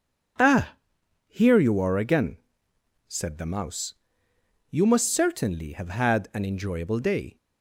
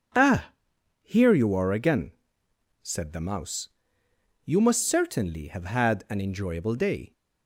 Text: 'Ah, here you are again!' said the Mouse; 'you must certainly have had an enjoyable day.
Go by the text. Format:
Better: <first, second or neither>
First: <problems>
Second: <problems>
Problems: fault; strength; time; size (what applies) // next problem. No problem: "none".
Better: neither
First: none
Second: none